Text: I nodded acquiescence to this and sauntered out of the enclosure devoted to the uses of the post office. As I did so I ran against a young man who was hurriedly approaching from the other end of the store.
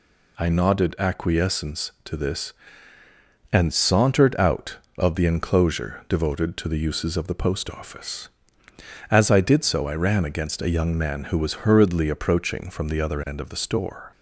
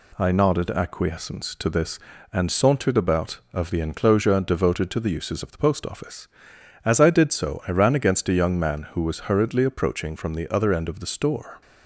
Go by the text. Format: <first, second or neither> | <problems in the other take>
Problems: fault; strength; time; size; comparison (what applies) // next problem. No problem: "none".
first | says "about" for "out"; at 2.9 s